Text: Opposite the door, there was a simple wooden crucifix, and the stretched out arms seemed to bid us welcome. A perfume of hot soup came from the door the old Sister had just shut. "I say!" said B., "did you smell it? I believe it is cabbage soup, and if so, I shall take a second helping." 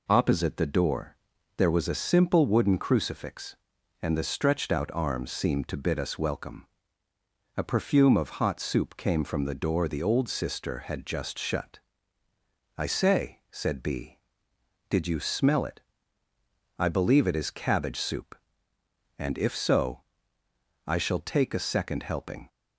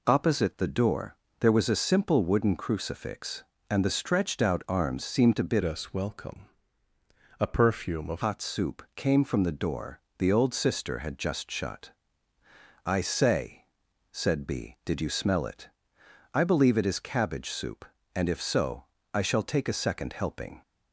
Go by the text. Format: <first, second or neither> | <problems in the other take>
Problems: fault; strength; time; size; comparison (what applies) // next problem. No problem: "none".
first | changes voice from "us" to "of"; from 5.6 to 8.2 s; 2.6 s long // pauses between "door" and "the"; slight; at 9.9 s; 0.18 s long